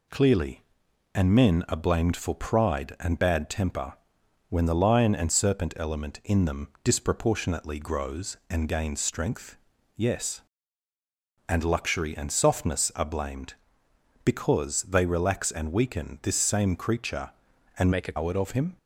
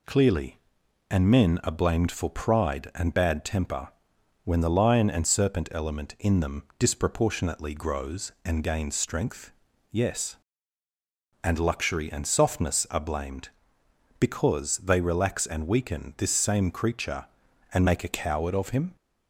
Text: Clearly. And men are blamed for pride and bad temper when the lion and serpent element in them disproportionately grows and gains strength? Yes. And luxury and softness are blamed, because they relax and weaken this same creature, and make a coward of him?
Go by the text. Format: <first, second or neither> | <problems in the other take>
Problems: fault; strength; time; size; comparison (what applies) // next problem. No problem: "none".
second | pauses between "temper" and "when"; noticeable; at 3.9 s; 0.56 s long; noticeable in the second // changes voice from "make" to "a"; from 17.9 to 18.1 s; 0.2 s long